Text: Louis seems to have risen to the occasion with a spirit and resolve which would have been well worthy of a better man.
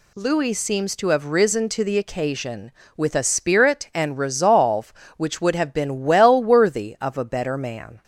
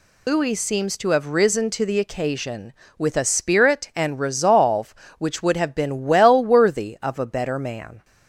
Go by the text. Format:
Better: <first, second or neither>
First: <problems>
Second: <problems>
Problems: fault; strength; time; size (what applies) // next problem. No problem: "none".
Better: first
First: none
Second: loses the start of "Louis"; at 0.2 s; 105 ms